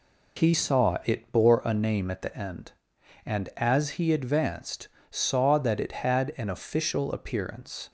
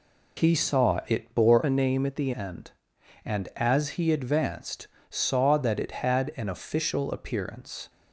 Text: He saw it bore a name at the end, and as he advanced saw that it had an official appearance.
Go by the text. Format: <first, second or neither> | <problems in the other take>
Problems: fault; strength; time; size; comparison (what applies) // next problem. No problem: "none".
first | changes voice from "a" to "the"; from 1.6 to 2.3 s; 0.7 s long // pauses between "advanced" and "saw"; slight; at 4.8 s; 0.20 s long; slight in the first